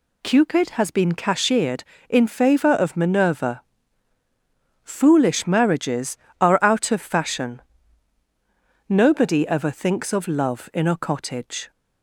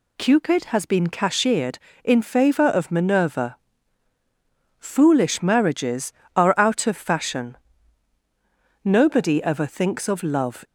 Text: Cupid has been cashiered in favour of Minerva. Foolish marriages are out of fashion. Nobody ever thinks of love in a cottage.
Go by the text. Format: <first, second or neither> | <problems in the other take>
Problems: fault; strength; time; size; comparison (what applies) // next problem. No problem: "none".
first | stops before "in a cottage"; at 10.6 s